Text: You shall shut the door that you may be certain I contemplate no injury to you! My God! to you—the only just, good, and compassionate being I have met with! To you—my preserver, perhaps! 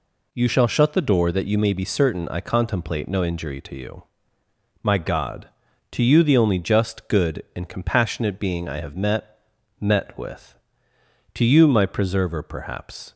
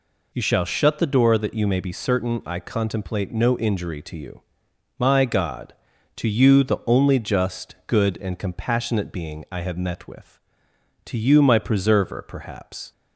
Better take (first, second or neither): second